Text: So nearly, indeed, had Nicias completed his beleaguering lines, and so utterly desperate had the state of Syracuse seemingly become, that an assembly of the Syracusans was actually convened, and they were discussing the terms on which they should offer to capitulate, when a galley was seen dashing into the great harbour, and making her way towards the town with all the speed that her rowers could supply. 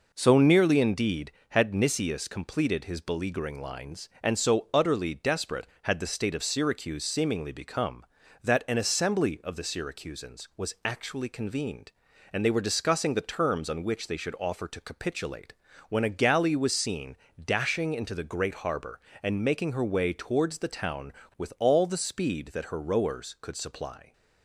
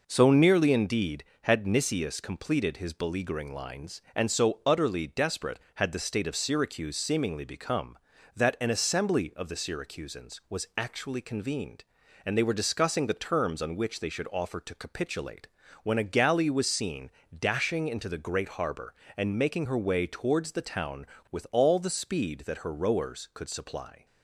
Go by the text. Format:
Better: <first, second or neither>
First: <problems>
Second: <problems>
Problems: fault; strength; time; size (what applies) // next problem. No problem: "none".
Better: neither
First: pauses between "seen" and "dashing"; slight; at 17.1 s; 0.28 s long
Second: pauses between "seen" and "dashing"; slight; at 17.0 s; 0.28 s long